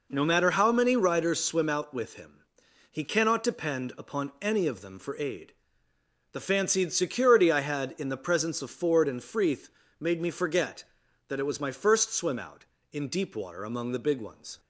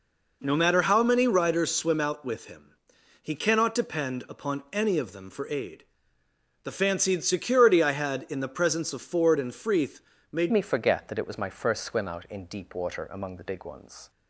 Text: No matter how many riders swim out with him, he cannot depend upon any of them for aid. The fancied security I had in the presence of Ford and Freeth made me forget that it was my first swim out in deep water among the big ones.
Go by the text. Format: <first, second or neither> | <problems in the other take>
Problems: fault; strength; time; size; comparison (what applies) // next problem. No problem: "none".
first | pauses between "Freeth" and "made"; slight; at 9.9 s; 0.32 s long; slight in the first // changes voice at "me"; from 10.4 s on; 3.6 s long